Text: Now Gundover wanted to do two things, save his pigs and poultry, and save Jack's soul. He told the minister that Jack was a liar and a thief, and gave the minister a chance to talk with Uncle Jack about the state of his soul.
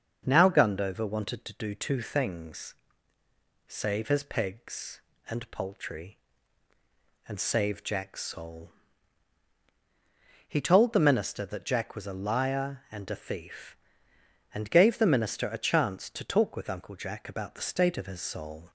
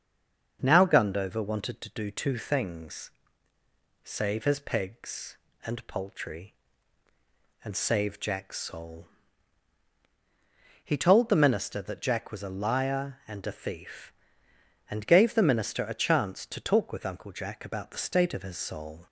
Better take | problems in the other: first | stays silent before the first word; slight; until 0.5 s; 0.5 s long // starts louder than the rest; until 1.6 s; 6.5 dB; also in the first

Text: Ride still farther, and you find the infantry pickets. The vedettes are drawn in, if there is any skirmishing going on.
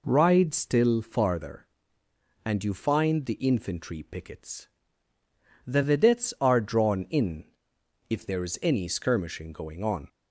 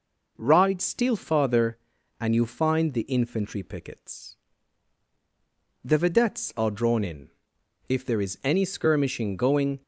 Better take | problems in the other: first | stops before "on"; at 9.8 s

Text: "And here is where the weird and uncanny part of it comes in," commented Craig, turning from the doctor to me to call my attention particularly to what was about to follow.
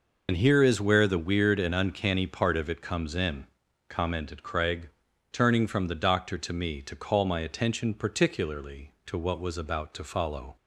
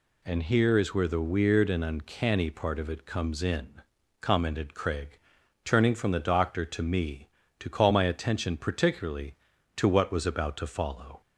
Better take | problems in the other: second | loses the start of "And"; at 0.2 s; 95 ms

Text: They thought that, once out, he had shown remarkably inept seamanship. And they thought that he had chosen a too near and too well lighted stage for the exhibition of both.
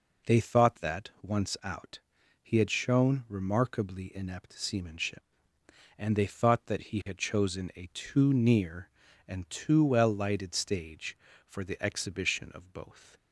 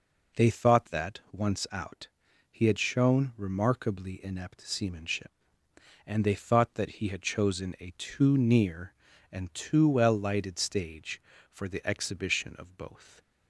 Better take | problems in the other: neither | none

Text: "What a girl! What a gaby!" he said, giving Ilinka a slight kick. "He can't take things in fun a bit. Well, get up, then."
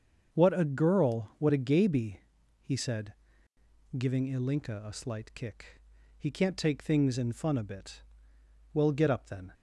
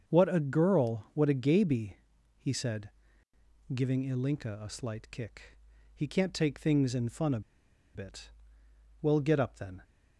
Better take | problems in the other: first | starts louder than the rest; until 1.1 s; 6.5 dB; also in the first // pauses between "a" and "bit"; noticeable; at 7.3 s; 0.54 s long

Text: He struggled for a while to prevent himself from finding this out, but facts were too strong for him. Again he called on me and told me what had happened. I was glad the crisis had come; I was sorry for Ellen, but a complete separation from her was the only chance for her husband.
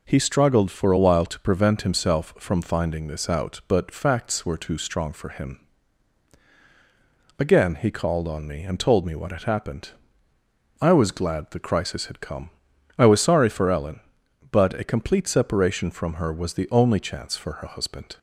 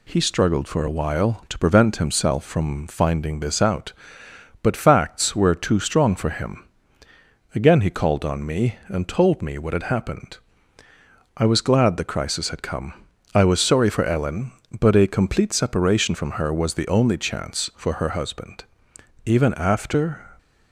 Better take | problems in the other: first | goes on to say "Even after"; noticeable; from 19.2 s on; 1.0 s long

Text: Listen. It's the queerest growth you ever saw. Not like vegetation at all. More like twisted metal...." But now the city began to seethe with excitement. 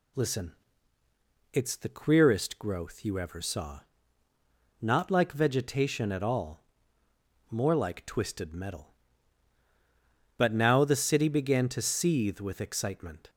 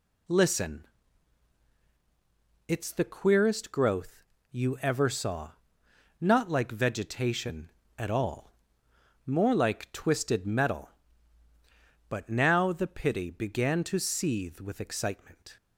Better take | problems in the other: first | pauses between "growth" and "you"; slight; at 4.2 s; 0.30 s long // says "pity" for "city"; at 12.8 s

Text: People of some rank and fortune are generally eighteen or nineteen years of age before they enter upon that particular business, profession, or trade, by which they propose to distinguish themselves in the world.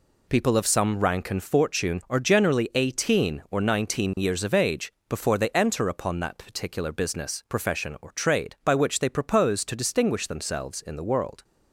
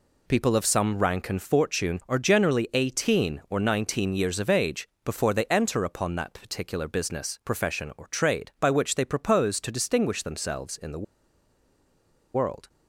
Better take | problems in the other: first | pauses between "age" and "before"; slight; at 4.8 s; 0.16 s long; slight in the first // pauses between "the" and "world"; strong; at 11.0 s; 1.3 s long

